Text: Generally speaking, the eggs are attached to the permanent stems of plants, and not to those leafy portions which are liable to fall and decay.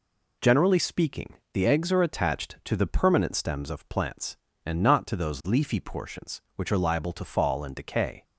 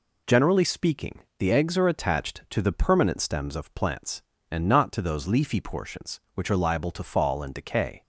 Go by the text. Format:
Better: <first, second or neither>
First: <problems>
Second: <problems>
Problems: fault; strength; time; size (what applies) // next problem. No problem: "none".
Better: neither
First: none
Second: none